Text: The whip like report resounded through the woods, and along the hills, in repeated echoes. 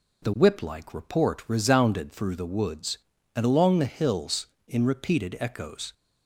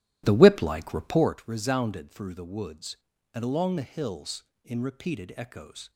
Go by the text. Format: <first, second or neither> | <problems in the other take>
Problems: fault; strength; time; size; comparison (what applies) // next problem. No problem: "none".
first | starts louder than the rest; strong; until 1.4 s; 15 dB